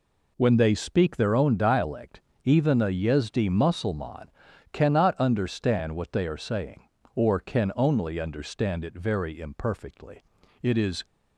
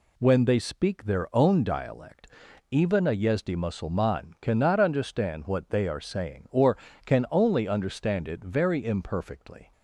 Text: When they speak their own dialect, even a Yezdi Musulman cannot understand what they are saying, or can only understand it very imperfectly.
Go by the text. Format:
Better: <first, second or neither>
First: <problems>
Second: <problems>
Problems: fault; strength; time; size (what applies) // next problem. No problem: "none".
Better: second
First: pauses between "Musulman" and "cannot"; noticeable; at 4.2 s; 0.46 s long // goes on to say "It is"; slight; from 10.6 s on; 0.42 s long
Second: none